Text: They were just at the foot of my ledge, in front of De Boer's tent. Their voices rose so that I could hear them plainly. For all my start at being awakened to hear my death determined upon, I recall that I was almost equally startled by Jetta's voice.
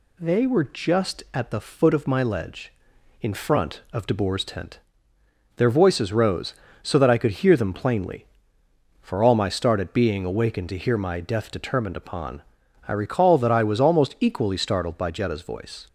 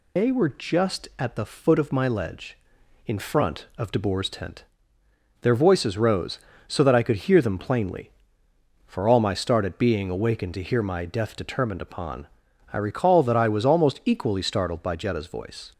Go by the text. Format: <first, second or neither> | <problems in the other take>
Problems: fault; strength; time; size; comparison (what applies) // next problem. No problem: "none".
first | loses the start of "They"; at 0.1 s; 115 ms